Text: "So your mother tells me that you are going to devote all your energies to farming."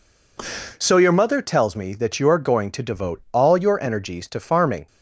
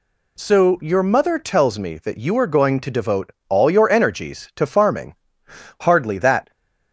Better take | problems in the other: first | pauses between "devote" and "all"; slight; at 3.3 s; 0.16 s long // goes on to say "Hardly that"; noticeable; from 5.7 s on; 0.72 s long

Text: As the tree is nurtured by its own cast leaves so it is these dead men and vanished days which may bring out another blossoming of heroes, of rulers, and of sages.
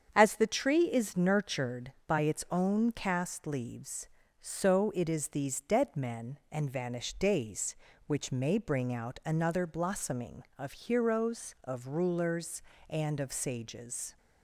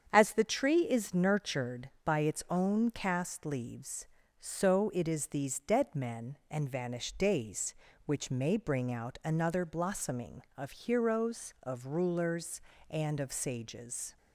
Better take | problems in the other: neither | starts louder than the rest; strong; the same in both

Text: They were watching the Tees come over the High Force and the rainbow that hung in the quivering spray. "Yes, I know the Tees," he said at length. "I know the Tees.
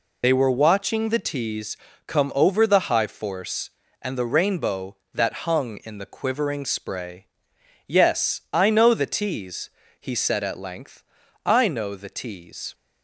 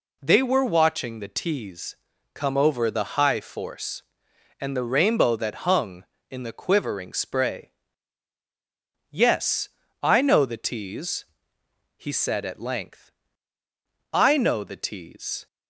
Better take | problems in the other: second | loses the start of "They"; at 0.2 s; 60 ms // pauses between "Tees" and "come"; slight; at 1.7 s; 0.30 s long; also in the second

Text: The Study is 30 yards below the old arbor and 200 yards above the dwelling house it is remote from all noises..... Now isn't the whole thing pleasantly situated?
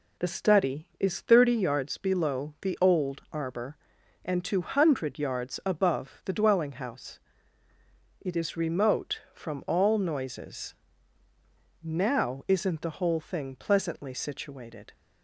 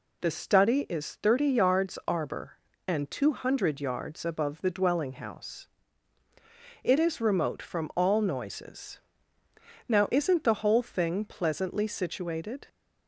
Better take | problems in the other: first | skips "below the old"; at 2.0 s // pauses between "house" and "it"; at 5.6 s; 1.1 s long; also in the first

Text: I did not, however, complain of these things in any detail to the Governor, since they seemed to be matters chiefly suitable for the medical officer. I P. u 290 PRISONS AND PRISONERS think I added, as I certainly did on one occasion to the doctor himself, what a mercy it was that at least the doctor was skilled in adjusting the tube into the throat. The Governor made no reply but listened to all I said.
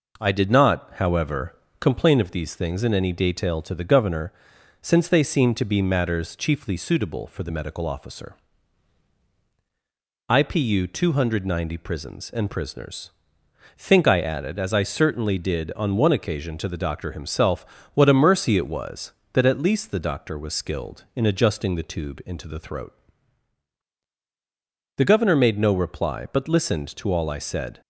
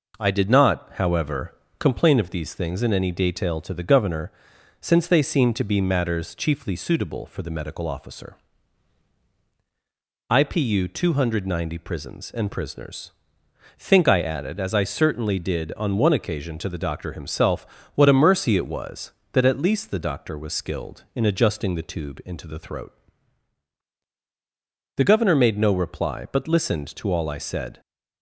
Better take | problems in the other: neither | pauses between "PRISONERS" and "think"; noticeable; the same in both

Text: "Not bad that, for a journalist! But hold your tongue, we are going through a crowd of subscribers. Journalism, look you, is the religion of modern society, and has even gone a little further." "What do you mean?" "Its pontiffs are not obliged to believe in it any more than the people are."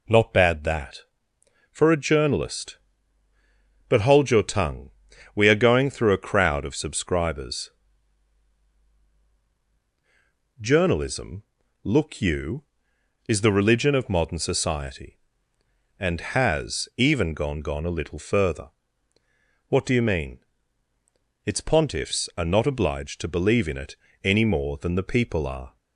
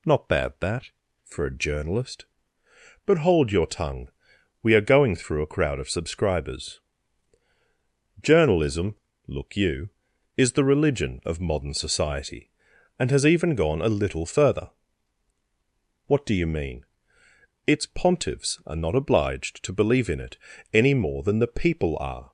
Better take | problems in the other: second | says "gone" twice; at 17.6 s // pauses between "it" and "any"; slight; at 23.9 s; 0.26 s long; slight in the second

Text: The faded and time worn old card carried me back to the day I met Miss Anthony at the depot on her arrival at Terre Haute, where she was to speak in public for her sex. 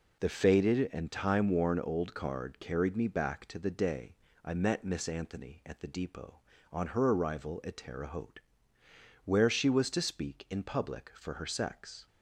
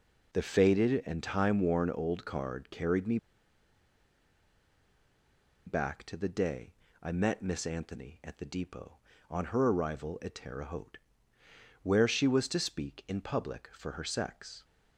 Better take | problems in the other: first | pauses between "me" and "back"; strong; at 3.1 s; 2.4 s long // pauses between "day" and "I"; slight; at 6.7 s; 0.26 s long; slight in the first

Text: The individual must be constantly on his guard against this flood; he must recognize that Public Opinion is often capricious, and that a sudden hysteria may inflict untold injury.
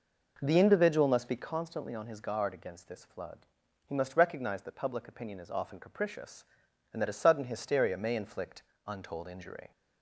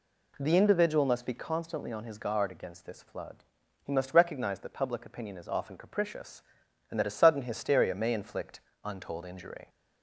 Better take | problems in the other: second | starts louder than the rest; noticeable; until 1.5 s; 5 dB // pauses between "inflict" and "untold"; slight; at 8.6 s; 0.24 s long; slight in the second

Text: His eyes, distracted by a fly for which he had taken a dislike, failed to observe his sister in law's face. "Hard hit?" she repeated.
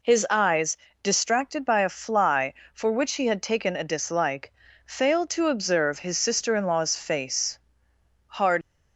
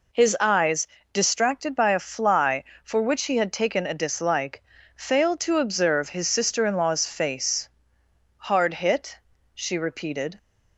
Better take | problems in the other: second | stops before "hit she repeated"; at 8.6 s

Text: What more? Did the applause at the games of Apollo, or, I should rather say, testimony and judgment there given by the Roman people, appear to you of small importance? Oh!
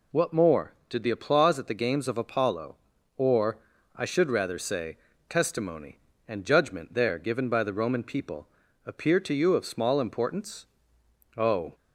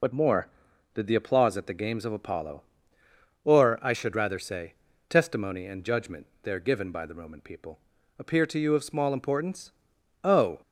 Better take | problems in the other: first | loses the start of "What"; at 0.0 s; 55 ms // pauses between "judgment" and "there"; slight; at 6.2 s; 0.18 s long

